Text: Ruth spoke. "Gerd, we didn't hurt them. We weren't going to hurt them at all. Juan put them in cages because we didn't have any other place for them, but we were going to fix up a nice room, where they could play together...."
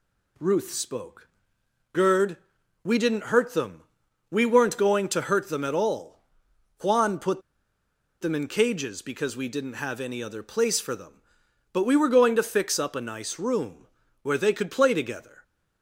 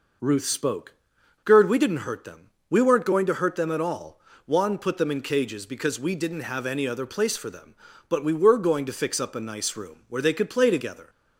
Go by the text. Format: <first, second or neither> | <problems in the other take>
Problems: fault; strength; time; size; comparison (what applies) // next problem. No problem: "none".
second | pauses between "put" and "them"; noticeable; at 7.4 s; 0.79 s long